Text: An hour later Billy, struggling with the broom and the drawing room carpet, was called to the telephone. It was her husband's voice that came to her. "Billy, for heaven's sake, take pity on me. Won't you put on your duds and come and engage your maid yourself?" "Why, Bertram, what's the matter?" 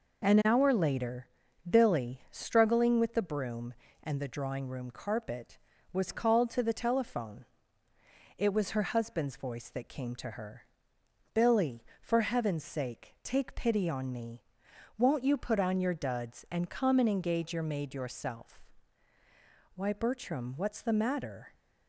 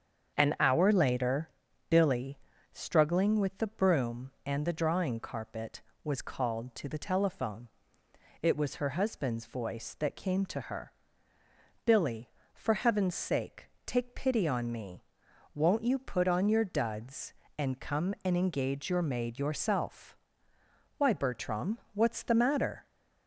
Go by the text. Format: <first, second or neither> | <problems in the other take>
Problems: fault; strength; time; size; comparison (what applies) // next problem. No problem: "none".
first | starts louder than the rest; strong; until 1.4 s; 7.5 dB // pauses between "later" and "Billy"; at 1.4 s; 0.40 s long; also in the first // skips "room"; at 5.1 s